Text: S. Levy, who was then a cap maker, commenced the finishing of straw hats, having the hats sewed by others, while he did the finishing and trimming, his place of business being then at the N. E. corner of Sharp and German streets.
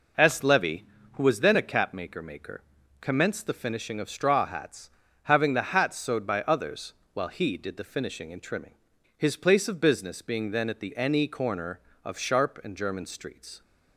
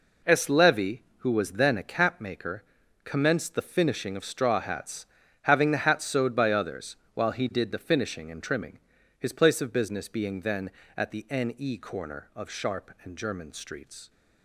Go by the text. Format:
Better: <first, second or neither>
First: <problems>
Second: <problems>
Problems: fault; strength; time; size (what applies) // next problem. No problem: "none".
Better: second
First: says "maker" twice; at 2.2 s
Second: none